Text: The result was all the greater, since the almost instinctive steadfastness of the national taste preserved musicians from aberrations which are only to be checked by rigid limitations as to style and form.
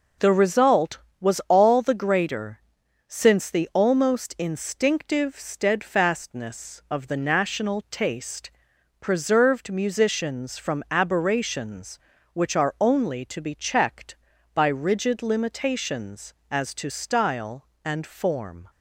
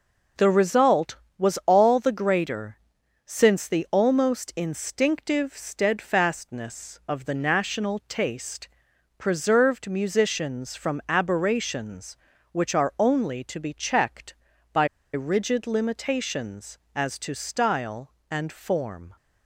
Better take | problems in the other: first | pauses between "taste" and "preserved"; noticeable; at 8.6 s; 0.48 s long; noticeable in the first // pauses between "by" and "rigid"; slight; at 14.8 s; 0.27 s long

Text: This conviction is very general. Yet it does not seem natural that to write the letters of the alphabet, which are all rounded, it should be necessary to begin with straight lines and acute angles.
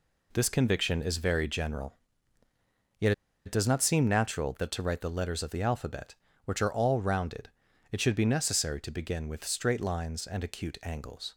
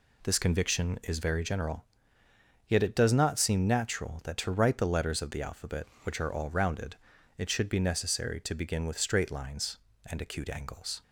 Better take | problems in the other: second | pauses between "Yet" and "it"; slight; at 3.1 s; 0.34 s long

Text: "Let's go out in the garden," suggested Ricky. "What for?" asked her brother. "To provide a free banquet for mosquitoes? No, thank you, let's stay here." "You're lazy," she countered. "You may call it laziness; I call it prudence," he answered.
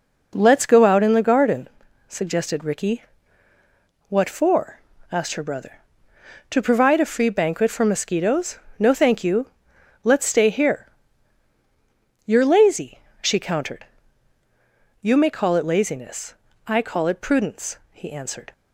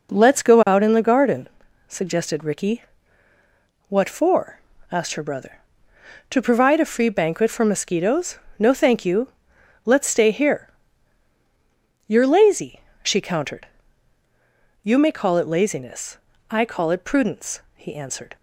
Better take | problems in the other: neither | none

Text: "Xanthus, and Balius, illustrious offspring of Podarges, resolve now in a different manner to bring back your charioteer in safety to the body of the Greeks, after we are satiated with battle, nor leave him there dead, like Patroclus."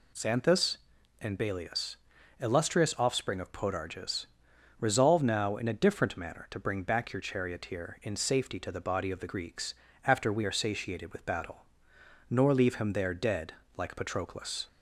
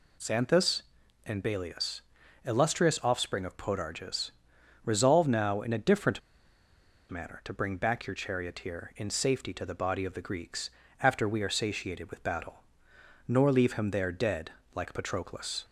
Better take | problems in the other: first | pauses between "different" and "manner"; noticeable; at 6.2 s; 0.90 s long

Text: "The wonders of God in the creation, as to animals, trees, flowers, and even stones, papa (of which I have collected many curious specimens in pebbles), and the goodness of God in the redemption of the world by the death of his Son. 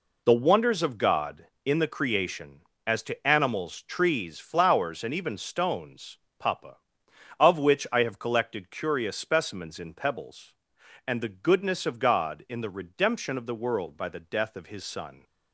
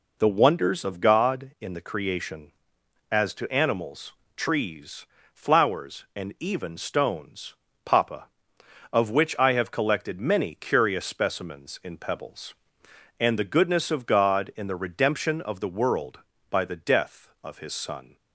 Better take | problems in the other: second | skips "many"; at 8.6 s

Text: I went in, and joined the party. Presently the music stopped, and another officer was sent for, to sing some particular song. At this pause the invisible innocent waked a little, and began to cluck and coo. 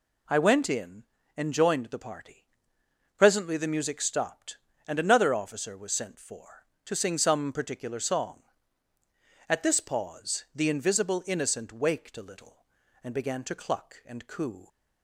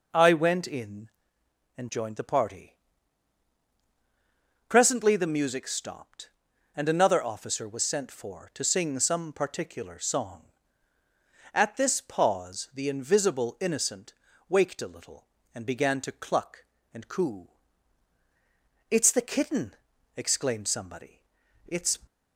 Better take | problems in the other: first | pauses between "innocent" and "waked"; at 14.1 s; 0.38 s long // goes on to say "It's the kitten exclaimed somebody It's"; strong; from 18.8 s on; 3.0 s long

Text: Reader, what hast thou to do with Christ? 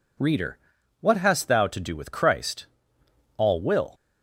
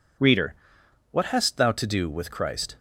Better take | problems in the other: second | goes on to say "All will"; from 3.3 s on; 0.56 s long

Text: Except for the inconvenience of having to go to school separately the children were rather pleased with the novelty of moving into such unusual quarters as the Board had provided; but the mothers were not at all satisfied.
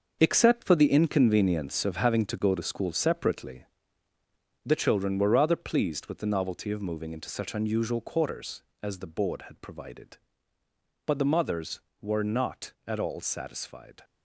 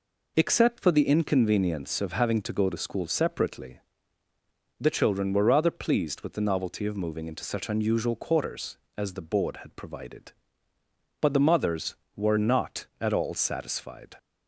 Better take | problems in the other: second | gets quieter; strong; throughout; 10 dB // pauses between "separately" and "the"; noticeable; at 3.6 s; 0.98 s long; noticeable in the second

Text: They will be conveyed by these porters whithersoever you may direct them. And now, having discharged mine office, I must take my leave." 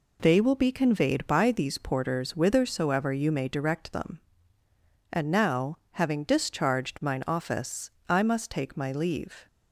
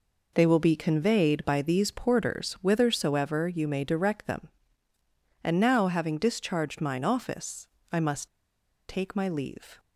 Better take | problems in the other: first | pauses between "must" and "take"; noticeable; at 8.2 s; 0.60 s long

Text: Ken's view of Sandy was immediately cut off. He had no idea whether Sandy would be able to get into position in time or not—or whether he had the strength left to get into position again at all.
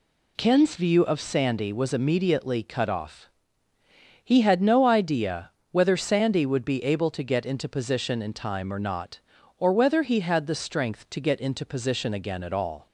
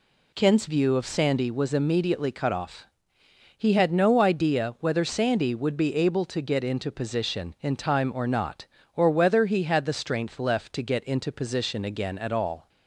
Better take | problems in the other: second | pauses between "idea" and "whether"; slight; at 5.5 s; 0.22 s long // skips "left"; at 11.0 s

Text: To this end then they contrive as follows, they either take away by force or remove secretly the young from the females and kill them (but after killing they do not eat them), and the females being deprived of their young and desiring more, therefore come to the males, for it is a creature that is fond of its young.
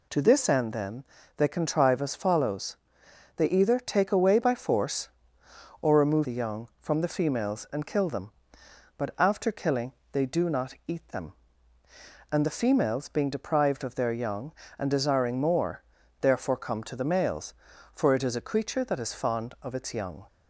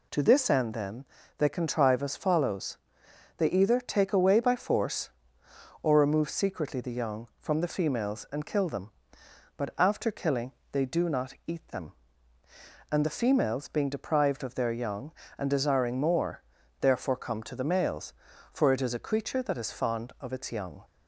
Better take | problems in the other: second | pauses between "then" and "they"; slight; at 1.0 s; 0.32 s long; slight in the second // skips "secretly"; at 6.2 s // pauses between "killing" and "they"; slight; at 9.9 s; 0.18 s long; slight in the second

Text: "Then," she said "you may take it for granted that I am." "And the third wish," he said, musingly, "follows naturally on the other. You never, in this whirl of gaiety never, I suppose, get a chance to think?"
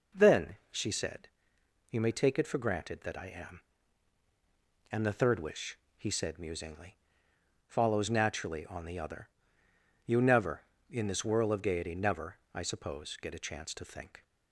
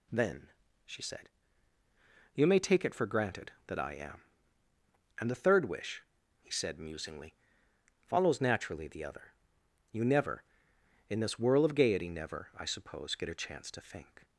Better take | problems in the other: first | pauses between "said" and "you"; at 1.2 s; 1.0 s long; noticeable in the first // skips "on"; at 8.8 s

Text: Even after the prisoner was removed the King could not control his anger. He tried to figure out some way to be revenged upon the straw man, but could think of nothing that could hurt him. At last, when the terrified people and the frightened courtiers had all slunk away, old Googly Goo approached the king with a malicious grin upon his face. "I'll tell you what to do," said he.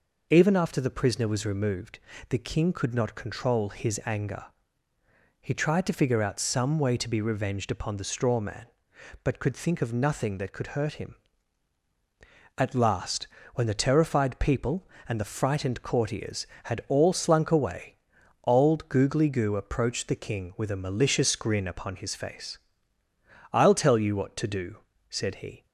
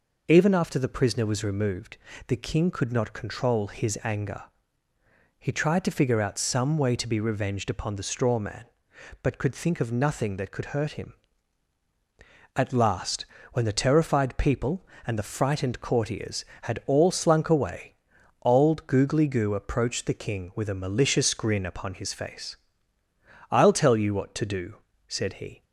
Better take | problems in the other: neither | pauses between "removed" and "the"; slight; the same in both

